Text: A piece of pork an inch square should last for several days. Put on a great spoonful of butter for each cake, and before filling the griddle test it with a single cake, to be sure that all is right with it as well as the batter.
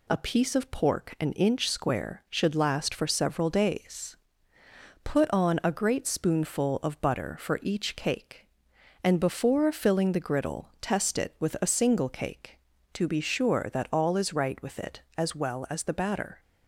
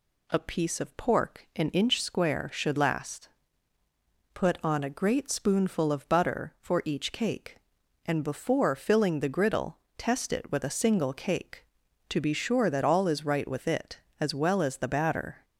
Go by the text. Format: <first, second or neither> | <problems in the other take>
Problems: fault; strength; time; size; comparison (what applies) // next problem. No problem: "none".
first | skips "for several days"; at 3.8 s // pauses between "griddle" and "test"; slight; at 9.7 s; 0.22 s long